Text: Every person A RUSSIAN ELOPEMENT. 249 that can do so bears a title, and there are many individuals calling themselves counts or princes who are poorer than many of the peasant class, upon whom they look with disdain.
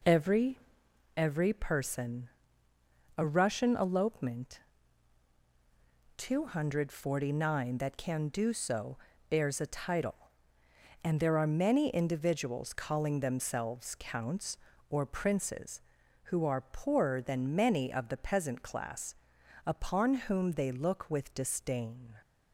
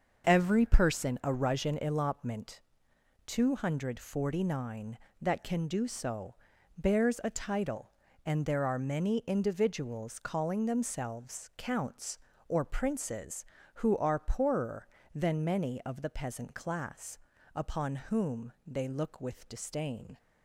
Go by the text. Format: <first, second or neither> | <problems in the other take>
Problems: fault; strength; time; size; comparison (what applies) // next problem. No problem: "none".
second | says "Every" twice; at 1.1 s // pauses between "person" and "A"; noticeable; at 2.2 s; 0.90 s long // pauses between "so" and "bears"; slight; at 8.9 s; 0.32 s long; also in the second